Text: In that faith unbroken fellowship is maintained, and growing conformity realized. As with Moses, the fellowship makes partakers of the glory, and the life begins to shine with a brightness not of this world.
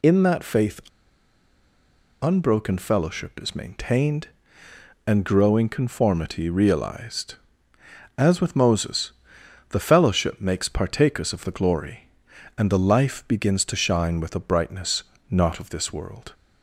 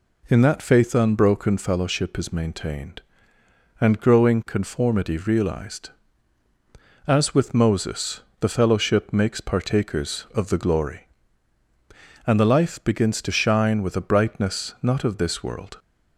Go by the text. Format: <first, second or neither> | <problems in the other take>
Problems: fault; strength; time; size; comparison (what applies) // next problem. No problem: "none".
second | pauses between "faith" and "unbroken"; strong; at 0.8 s; 1.4 s long // pauses between "brightness" and "not"; slight; at 15.0 s; 0.28 s long